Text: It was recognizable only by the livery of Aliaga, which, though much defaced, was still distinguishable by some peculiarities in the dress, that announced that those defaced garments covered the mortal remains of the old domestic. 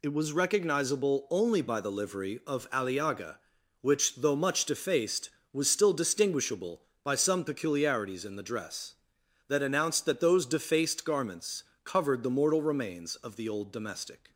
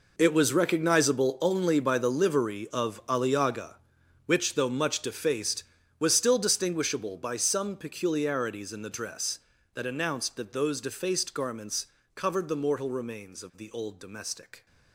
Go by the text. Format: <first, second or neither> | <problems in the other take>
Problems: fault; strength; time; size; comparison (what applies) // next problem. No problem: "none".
first | gets quieter; strong; throughout; 14.5 dB // pauses between "garments" and "covered"; slight; at 11.8 s; 0.28 s long; slight in the first